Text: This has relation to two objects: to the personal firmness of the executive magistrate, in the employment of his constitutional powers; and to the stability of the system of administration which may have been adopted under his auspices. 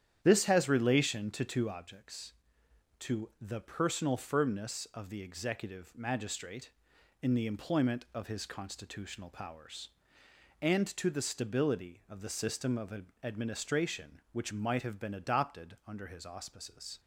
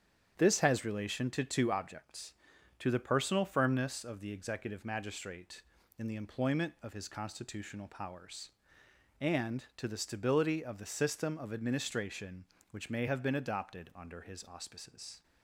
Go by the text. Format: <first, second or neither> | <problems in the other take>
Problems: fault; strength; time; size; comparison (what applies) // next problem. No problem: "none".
second | starts louder than the rest; strong; until 1.2 s; 9.5 dB; strong in the second // pauses between "of" and "administration"; slight; at 13.0 s; 0.18 s long // says "might" for "may"; at 14.5 s